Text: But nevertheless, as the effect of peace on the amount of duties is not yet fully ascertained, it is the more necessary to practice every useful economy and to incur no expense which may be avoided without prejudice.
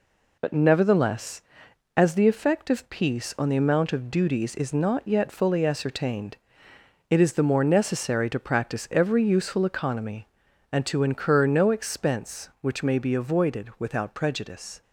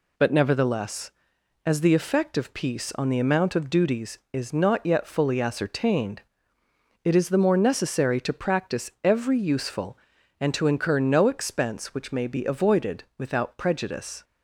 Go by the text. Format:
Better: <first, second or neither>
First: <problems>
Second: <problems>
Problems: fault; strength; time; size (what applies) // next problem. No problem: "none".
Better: first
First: none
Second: skips "economy"; at 10.1 s